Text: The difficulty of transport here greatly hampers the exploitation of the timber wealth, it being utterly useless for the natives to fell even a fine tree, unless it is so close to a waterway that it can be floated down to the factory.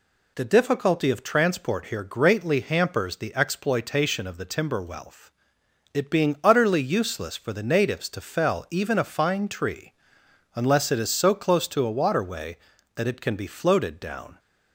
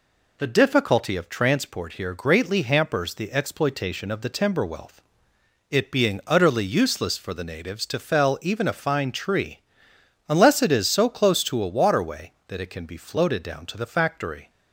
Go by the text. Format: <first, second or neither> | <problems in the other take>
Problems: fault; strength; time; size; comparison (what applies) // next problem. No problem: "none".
second | stops before "to the factory"; at 14.3 s